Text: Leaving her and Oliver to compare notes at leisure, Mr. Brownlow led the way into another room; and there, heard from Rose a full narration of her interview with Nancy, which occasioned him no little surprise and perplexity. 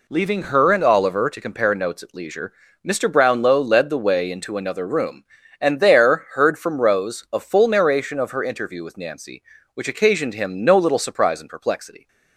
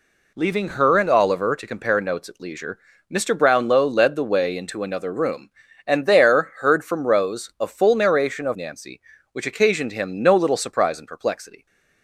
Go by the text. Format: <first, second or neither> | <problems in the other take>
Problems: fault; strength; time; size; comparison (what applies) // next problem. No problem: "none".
first | skips "her interview with"; at 8.5 s